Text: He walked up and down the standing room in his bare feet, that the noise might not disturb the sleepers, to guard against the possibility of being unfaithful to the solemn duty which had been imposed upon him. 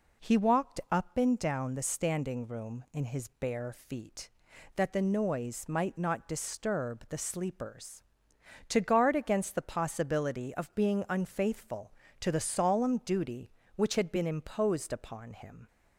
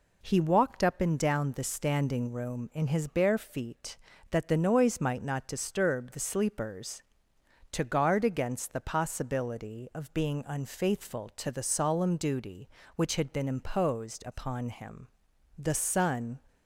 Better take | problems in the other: first | goes on to say "The sun"; noticeable; from 15.5 s on; 0.84 s long

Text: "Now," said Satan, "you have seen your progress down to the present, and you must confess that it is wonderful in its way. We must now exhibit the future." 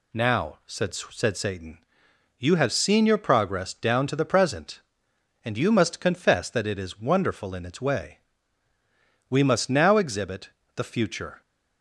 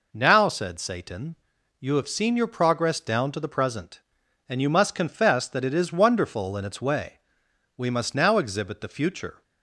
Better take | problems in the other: second | says "said" twice; at 0.9 s // pauses between "exhibit" and "the"; slight; at 10.5 s; 0.26 s long

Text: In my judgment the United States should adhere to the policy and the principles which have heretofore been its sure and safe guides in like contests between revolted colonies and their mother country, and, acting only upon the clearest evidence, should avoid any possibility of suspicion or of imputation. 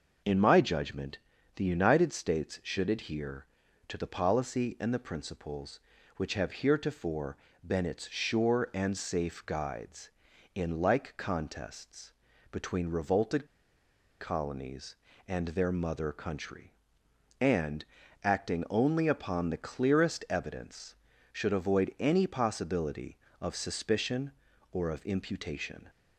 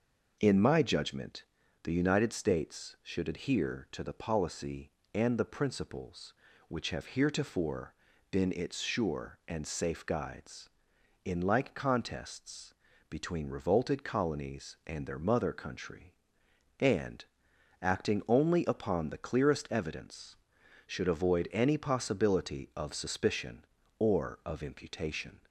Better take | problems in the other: second | pauses between "judgment" and "the"; at 1.1 s; 0.38 s long; also in the second // pauses between "heretofore" and "been"; slight; at 7.3 s; 0.32 s long; also in the second // pauses between "contests" and "between"; at 12.1 s; 0.40 s long; slight in the second // pauses between "revolted" and "colonies"; noticeable; at 13.4 s; 0.73 s long

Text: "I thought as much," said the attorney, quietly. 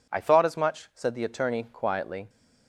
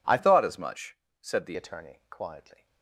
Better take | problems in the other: first | changes voice from "thought" to "the"; from 0.1 to 1.5 s; 1.4 s long

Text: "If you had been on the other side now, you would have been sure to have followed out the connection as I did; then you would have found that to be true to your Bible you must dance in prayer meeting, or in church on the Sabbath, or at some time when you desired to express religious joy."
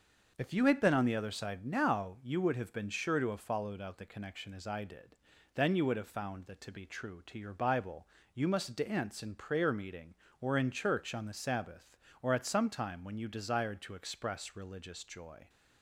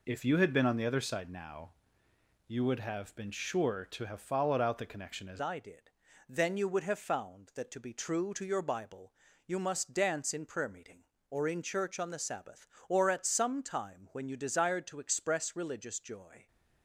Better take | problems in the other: first | changes voice at "I"; from 5.3 s on; 11.1 s long // pauses between "Bible" and "you"; slight; at 9.1 s; 0.32 s long; slight in the first

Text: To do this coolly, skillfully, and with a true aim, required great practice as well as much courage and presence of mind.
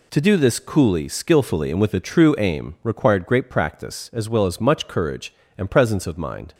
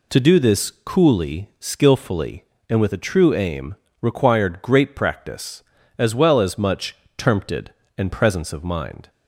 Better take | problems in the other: first | says "termpted" for "courage"; at 7.1 s

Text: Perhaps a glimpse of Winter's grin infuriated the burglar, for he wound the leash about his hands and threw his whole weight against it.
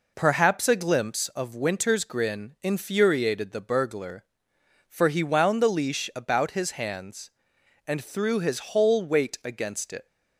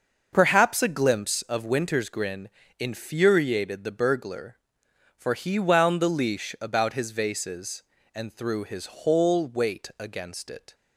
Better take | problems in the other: first | starts louder than the rest; until 1.3 s; 6.5 dB // pauses between "grin" and "infuriated"; slight; at 2.4 s; 0.32 s long // says "vases" for "hands"; at 7.1 s

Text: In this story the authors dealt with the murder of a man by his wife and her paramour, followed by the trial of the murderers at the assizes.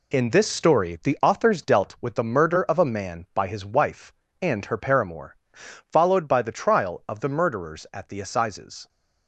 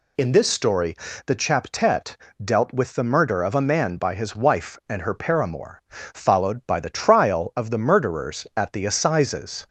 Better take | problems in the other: first | pauses between "story" and "the"; slight; at 0.9 s; 0.32 s long // says "chaptet" for "authors"; at 1.3 s

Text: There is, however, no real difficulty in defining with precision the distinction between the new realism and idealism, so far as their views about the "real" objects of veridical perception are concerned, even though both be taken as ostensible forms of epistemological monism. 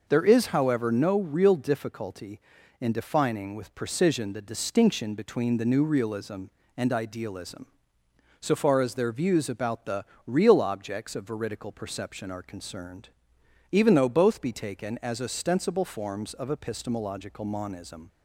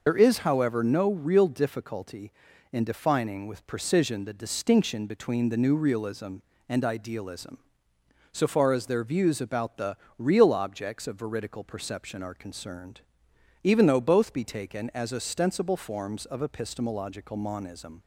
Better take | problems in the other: first | loses the start of "There"; at 0.0 s; 65 ms // pauses between "the" and "real"; slight; at 9.9 s; 0.20 s long; slight in the first

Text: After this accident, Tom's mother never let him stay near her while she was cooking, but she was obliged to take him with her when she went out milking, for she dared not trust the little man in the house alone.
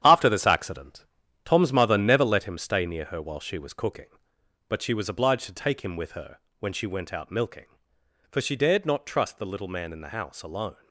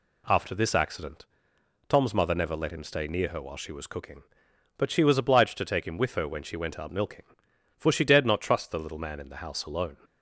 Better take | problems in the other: second | gets quieter; strong; throughout; 8.5 dB // pauses between "her" and "when"; slight; at 6.3 s; 0.20 s long

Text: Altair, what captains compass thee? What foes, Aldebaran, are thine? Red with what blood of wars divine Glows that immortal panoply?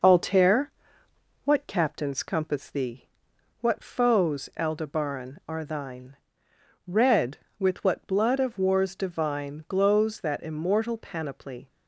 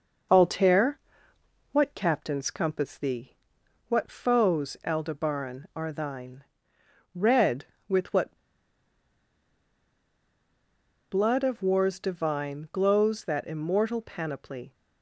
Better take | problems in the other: first | pauses between "what" and "blood"; strong; at 8.3 s; 2.7 s long

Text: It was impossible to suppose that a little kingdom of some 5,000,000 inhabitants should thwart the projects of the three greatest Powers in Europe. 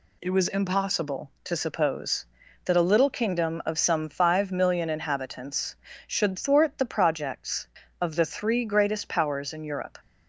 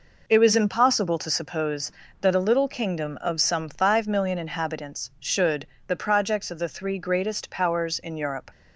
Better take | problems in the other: first | skips "thwart"; at 5.7 s

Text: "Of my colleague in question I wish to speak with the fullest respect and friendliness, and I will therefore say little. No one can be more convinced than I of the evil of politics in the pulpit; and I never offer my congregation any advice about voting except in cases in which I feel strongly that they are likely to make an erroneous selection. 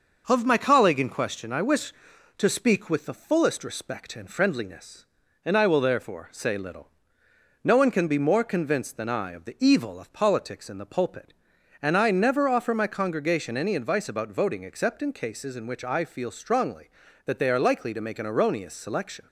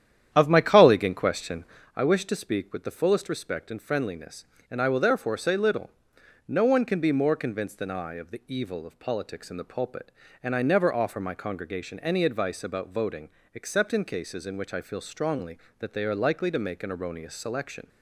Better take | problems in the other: first | starts louder than the rest; strong; until 1.9 s; 10 dB // pauses between "question" and "I"; slight; at 1.6 s; 0.28 s long // pauses between "voting" and "except"; slight; at 13.2 s; 0.26 s long

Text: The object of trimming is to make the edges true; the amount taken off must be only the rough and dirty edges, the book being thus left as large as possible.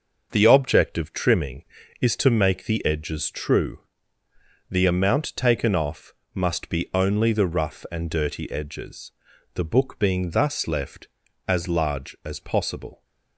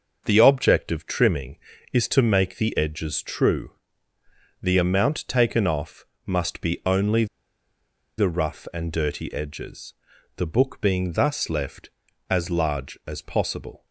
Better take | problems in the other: first | starts louder than the rest; noticeable; until 1.2 s; 6 dB; noticeable in the first // pauses between "off" and "must"; slight; at 6.0 s; 0.20 s long; slight in the first // pauses between "only" and "the"; noticeable; at 7.2 s; 0.92 s long

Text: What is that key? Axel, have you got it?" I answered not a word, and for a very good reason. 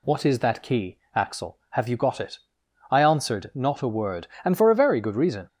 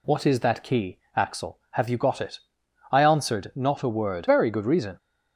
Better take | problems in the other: first | skips "and for a"; at 4.2 s

